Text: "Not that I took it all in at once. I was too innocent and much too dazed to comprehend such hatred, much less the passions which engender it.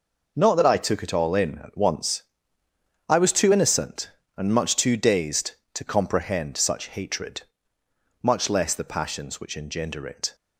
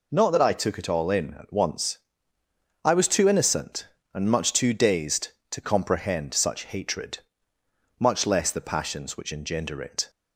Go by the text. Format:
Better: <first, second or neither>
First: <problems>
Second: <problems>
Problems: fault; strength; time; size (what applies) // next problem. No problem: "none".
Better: second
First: gets quieter; strong; throughout; 10 dB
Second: none